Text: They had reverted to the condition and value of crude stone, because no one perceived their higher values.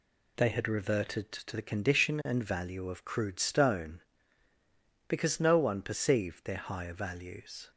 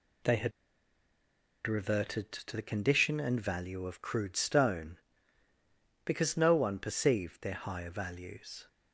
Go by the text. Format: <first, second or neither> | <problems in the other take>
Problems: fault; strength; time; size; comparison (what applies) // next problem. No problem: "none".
first | pauses between "had" and "reverted"; at 0.5 s; 1.1 s long